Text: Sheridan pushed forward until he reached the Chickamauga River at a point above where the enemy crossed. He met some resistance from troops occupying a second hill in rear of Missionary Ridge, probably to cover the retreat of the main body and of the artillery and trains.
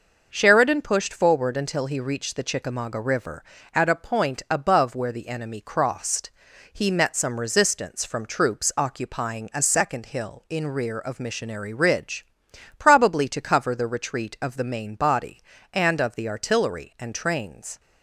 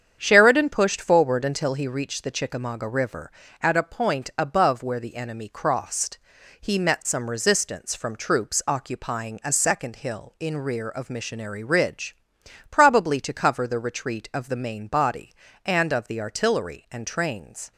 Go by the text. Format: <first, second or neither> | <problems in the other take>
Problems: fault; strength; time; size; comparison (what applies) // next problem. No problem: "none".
first | starts louder than the rest; strong; until 1.9 s; 8 dB